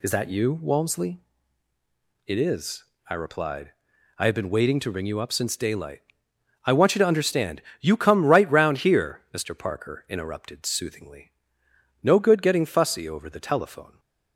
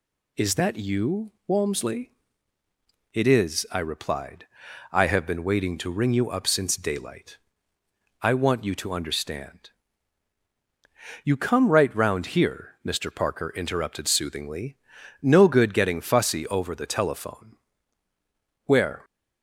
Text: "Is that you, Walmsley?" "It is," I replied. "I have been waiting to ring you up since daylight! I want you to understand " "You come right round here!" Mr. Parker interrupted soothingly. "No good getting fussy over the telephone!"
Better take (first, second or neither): first